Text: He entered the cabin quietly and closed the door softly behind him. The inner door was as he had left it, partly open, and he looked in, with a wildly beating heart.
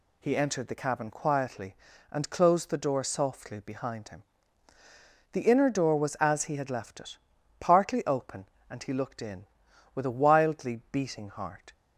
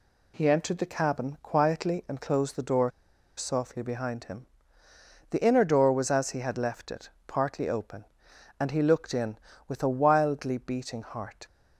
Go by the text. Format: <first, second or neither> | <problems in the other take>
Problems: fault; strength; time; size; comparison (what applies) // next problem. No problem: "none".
first | pauses between "door" and "softly"; noticeable; at 2.9 s; 0.46 s long